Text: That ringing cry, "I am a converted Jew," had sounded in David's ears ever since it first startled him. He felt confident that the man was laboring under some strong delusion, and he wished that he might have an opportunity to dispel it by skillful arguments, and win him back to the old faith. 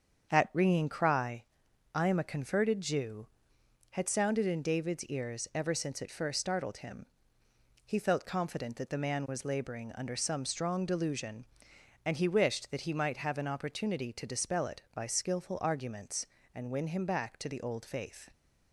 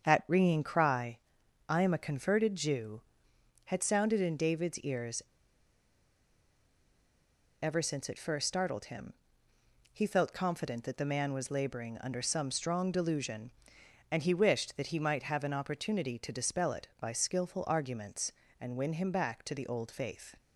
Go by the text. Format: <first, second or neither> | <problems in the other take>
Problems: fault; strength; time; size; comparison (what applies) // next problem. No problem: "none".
first | starts louder than the rest; strong; until 1.1 s; 7 dB; strong in the first // pauses between "ears" and "ever"; strong; at 5.2 s; 2.4 s long